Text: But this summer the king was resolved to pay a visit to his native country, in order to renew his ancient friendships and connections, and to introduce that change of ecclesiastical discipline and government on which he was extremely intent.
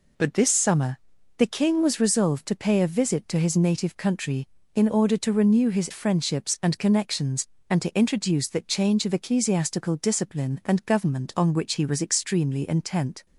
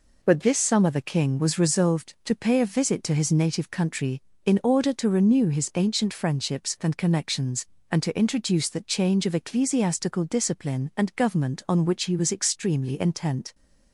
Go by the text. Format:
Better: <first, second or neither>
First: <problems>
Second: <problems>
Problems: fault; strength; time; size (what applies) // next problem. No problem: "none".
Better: second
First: pauses between "summer" and "the"; at 0.9 s; 0.40 s long // skips "ancient"; at 5.9 s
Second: none